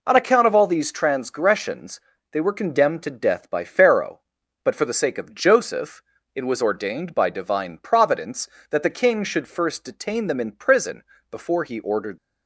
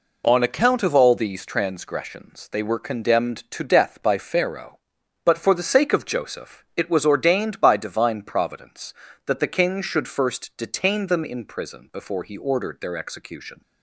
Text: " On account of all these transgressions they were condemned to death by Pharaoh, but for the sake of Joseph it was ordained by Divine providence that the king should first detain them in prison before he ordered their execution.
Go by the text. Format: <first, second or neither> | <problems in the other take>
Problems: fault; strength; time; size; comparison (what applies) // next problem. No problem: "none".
second | pauses between "transgressions" and "they"; slight; at 1.9 s; 0.32 s long // pauses between "Joseph" and "it"; slight; at 6.0 s; 0.32 s long // pauses between "prison" and "before"; slight; at 11.0 s; 0.26 s long // stops before "their execution"; at 12.1 s